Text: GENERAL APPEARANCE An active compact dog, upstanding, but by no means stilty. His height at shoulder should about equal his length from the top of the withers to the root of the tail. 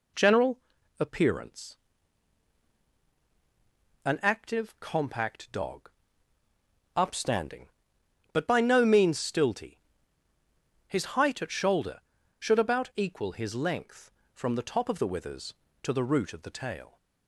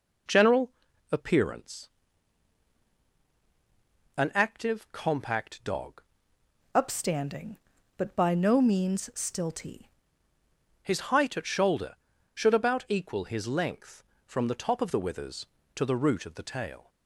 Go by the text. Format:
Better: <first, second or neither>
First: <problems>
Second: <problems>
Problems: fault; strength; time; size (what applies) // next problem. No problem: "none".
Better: first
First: pauses between "GENERAL" and "APPEARANCE"; at 0.5 s; 0.40 s long // pauses between "APPEARANCE" and "An"; strong; at 1.7 s; 2.3 s long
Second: pauses between "GENERAL" and "APPEARANCE"; at 0.7 s; 0.40 s long // pauses between "APPEARANCE" and "An"; strong; at 1.8 s; 2.3 s long // changes voice from "upstanding" to "stilty"; from 6.7 to 9.8 s; 3.1 s long